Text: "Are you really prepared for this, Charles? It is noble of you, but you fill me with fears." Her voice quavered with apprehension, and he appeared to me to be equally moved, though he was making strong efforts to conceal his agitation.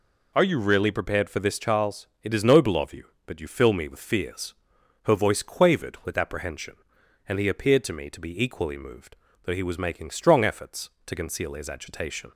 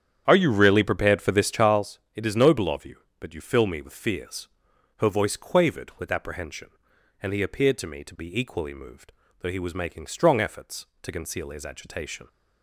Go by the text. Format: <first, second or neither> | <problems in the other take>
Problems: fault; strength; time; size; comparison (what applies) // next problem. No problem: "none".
first | starts louder than the rest; strong; until 1.9 s; 9 dB